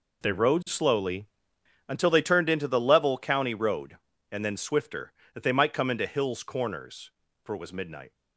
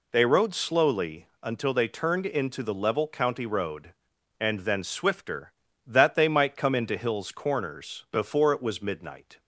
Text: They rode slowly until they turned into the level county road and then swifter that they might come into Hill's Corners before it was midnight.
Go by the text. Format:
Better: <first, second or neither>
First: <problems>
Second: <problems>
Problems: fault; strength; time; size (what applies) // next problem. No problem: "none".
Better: second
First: pauses between "slowly" and "until"; noticeable; at 1.2 s; 0.60 s long // says "for" for "before"; at 7.4 s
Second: none